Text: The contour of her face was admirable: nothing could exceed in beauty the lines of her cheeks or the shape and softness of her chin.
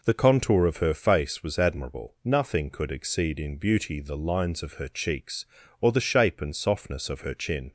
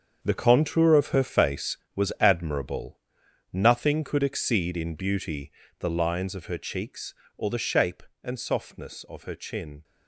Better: first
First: none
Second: gets quieter; strong; throughout; 11.5 dB // pauses between "beauty" and "the"; slight; at 5.5 s; 0.28 s long

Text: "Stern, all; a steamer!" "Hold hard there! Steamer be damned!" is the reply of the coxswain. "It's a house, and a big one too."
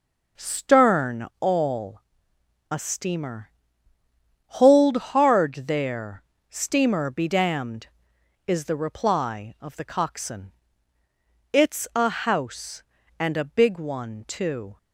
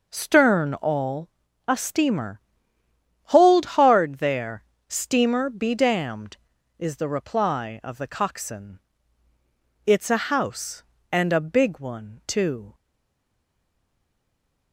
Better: first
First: none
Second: stays silent after the last word; noticeable; from 12.7 s on; 2.0 s long

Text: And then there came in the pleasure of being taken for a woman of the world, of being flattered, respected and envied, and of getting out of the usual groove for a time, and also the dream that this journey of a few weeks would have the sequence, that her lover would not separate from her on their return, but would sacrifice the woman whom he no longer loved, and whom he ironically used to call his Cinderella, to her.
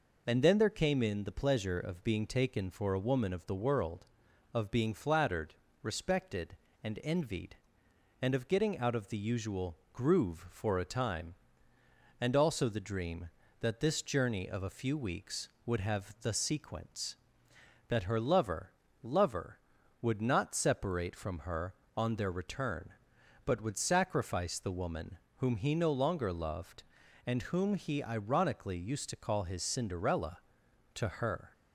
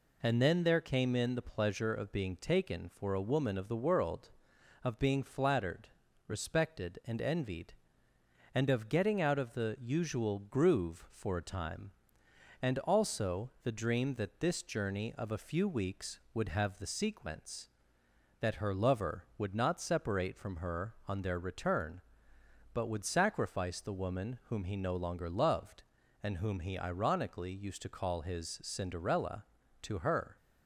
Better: second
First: pauses between "usual" and "groove"; slight; at 9.7 s; 0.16 s long // says "lover" twice; at 19.0 s // pauses between "woman" and "whom"; slight; at 25.1 s; 0.18 s long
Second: none

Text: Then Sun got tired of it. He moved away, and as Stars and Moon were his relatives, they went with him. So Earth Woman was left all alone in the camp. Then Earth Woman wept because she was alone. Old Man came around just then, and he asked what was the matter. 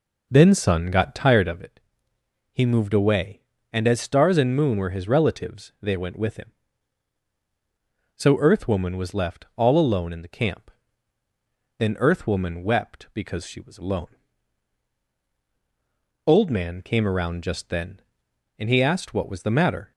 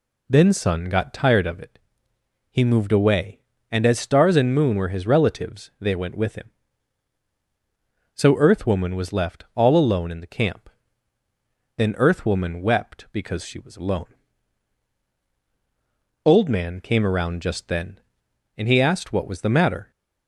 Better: second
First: starts louder than the rest; noticeable; until 1.6 s; 4.5 dB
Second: none

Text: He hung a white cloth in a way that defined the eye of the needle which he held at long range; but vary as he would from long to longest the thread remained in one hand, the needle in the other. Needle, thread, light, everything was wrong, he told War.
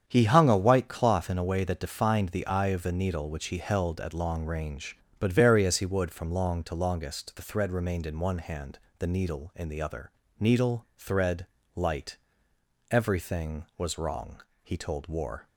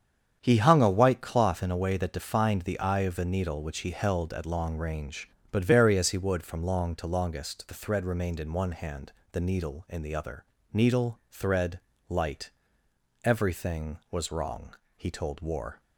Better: neither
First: starts louder than the rest; strong; until 1.0 s; 8 dB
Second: starts louder than the rest; strong; until 1.4 s; 8 dB

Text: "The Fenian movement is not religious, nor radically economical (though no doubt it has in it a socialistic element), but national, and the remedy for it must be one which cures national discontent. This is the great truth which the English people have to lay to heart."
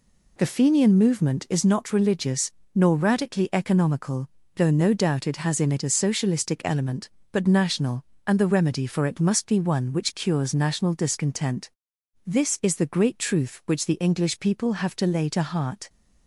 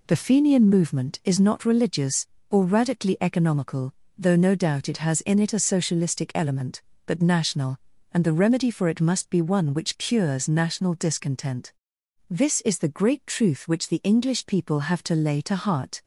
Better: first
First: none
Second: says "or" for "nor"; at 2.5 s

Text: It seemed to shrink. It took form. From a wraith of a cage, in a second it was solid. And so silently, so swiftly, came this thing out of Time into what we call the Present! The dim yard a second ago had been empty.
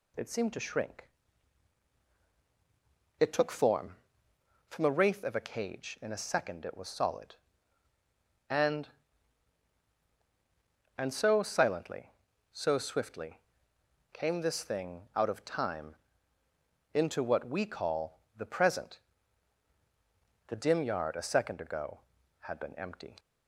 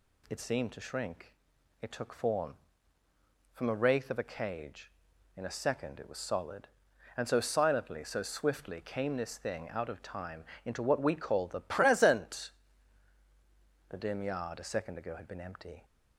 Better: second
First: says "And" twice; at 10.9 s // pauses between "Time" and "into"; noticeable; at 15.9 s; 0.96 s long // pauses between "call" and "the"; slight; at 18.1 s; 0.16 s long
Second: pauses between "Time" and "into"; slight; at 10.4 s; 0.22 s long

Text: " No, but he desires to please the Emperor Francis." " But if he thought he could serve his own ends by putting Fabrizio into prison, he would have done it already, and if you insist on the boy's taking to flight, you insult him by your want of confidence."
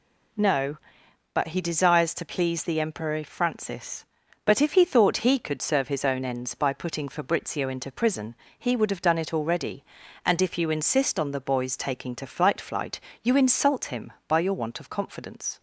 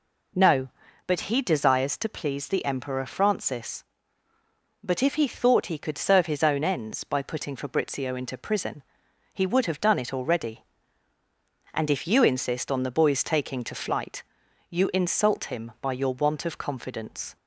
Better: second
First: says "flight" twice; at 12.6 s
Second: none

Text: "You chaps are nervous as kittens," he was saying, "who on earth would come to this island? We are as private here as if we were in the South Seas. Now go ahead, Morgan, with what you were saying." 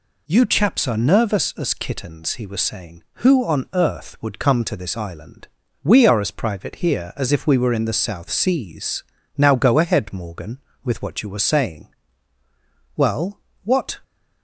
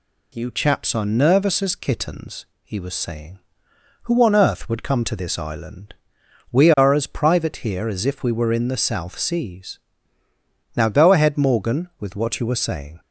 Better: second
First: goes on to say "Well what"; noticeable; from 12.9 s on; 1.0 s long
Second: none

